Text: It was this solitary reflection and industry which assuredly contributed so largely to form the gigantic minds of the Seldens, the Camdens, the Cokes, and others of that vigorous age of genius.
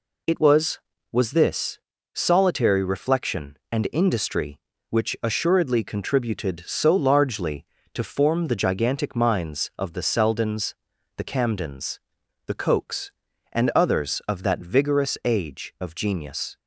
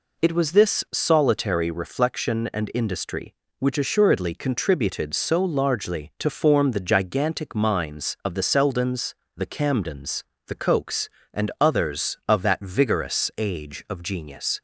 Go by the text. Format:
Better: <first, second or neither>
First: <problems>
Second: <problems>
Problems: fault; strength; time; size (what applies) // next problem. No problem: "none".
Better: second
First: says "was" twice; at 1.1 s // pauses between "this" and "solitary"; slight; at 1.7 s; 0.34 s long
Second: none